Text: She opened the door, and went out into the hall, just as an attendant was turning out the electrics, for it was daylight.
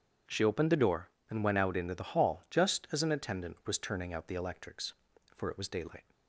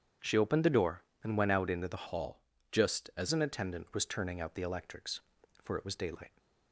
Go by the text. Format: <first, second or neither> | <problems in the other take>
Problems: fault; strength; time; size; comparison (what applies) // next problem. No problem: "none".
first | starts louder than the rest; strong; until 1.4 s; 8 dB // changes voice from "hall" to "as"; from 2.0 to 3.2 s; 1.2 s long